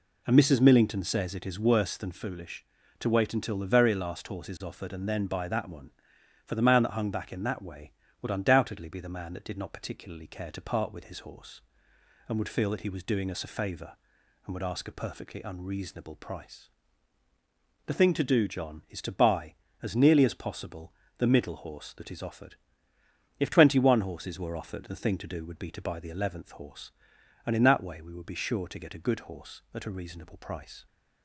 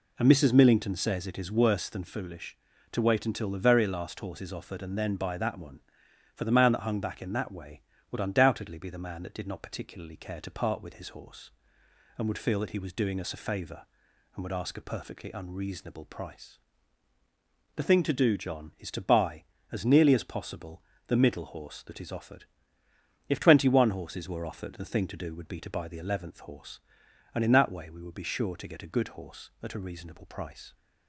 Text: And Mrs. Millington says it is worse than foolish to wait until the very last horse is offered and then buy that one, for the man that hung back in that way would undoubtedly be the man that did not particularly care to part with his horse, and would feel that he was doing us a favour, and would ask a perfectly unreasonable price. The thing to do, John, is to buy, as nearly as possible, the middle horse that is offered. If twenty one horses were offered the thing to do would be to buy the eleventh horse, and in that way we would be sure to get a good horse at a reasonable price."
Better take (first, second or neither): neither